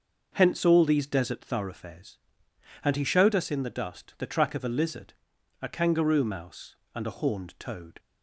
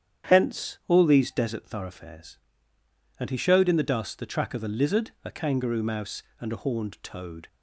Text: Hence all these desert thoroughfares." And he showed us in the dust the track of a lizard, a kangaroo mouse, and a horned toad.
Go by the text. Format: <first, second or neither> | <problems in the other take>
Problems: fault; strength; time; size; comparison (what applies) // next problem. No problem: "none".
first | starts louder than the rest; strong; until 1.3 s; 9 dB; noticeable in the first // skips "us"; at 3.6 s